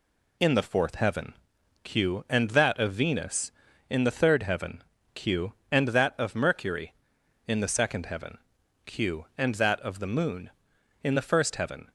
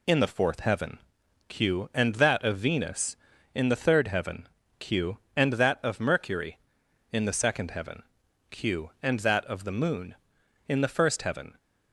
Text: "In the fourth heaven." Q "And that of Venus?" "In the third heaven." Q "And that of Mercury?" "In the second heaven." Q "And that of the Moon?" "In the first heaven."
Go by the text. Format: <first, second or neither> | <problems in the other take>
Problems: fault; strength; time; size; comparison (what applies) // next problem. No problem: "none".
neither | none